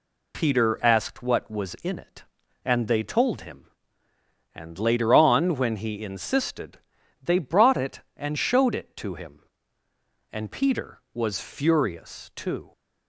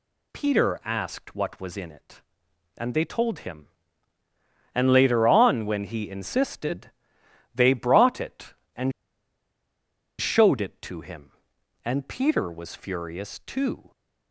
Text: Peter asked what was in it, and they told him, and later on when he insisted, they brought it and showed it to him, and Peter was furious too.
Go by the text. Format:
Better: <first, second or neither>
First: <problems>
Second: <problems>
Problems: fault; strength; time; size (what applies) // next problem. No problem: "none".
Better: first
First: none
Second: pauses between "and" and "showed"; strong; at 8.9 s; 1.2 s long